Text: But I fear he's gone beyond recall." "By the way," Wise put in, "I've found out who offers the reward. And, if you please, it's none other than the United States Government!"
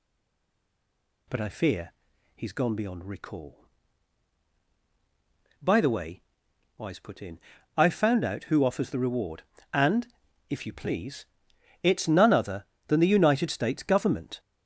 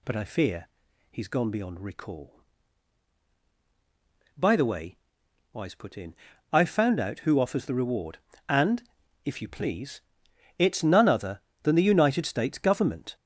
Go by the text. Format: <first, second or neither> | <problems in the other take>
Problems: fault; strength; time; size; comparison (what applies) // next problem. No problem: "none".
second | stays silent before the first word; noticeable; until 1.2 s; 1.2 s long // pauses between "fear" and "he's"; at 1.9 s; 0.44 s long; also in the second